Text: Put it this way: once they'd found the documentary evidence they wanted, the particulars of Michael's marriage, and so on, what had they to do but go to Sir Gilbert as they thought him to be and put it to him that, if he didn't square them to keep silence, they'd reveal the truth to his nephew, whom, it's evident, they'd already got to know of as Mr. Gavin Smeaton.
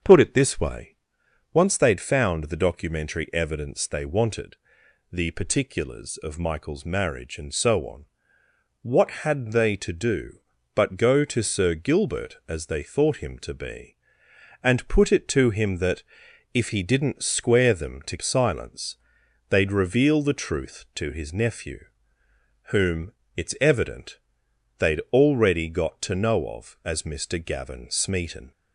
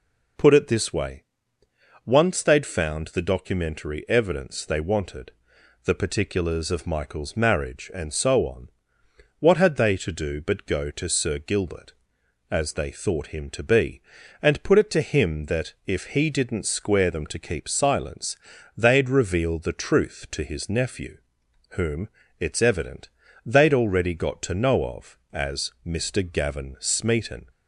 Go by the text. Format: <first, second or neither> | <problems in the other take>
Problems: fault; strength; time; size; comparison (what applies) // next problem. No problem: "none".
second | starts louder than the rest; until 1.6 s; 6.5 dB // skips "keep"; at 18.1 s